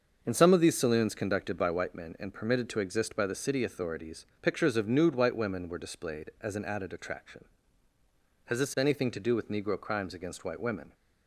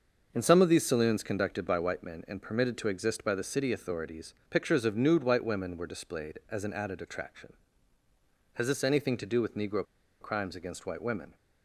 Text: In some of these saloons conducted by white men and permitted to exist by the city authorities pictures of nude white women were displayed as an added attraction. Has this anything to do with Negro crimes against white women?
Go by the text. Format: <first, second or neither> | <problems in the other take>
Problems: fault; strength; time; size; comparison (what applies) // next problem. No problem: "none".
first | starts louder than the rest; until 1.3 s; 6.5 dB; also in the first // pauses between "authorities" and "pictures"; slight; at 4.3 s; 0.16 s long; slight in the first // pauses between "Negro" and "crimes"; at 9.8 s; 0.37 s long